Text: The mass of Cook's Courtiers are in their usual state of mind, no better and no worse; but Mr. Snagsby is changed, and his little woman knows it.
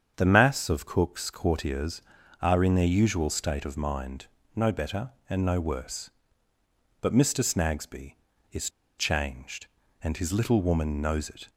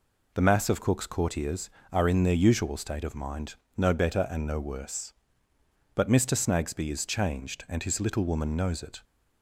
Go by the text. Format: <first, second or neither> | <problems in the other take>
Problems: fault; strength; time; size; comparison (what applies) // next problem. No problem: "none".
second | starts louder than the rest; strong; until 1.1 s; 7.5 dB // pauses between "is" and "changed"; slight; at 8.6 s; 0.29 s long